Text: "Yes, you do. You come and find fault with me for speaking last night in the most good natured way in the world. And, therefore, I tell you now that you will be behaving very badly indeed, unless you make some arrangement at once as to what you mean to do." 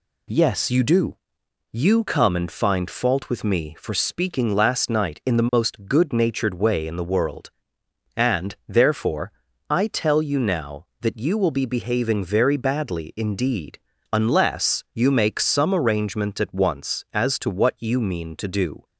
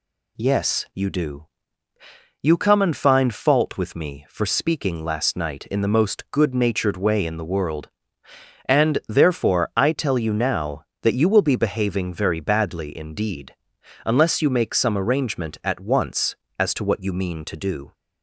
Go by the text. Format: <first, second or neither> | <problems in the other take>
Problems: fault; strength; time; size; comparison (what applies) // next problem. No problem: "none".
neither | none